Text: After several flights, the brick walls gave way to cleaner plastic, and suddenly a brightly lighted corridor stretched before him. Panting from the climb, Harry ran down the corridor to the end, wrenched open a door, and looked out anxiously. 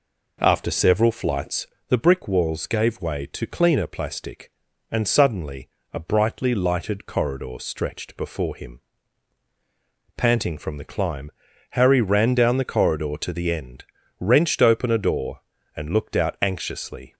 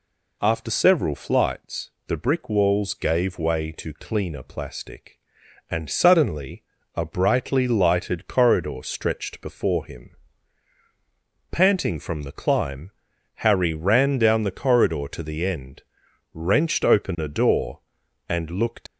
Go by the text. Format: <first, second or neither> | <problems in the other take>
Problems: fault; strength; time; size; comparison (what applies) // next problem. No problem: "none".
first | pauses between "suddenly" and "a"; slight; at 6.6 s; 0.32 s long; slight in the first // stops before "out anxiously"; at 18.8 s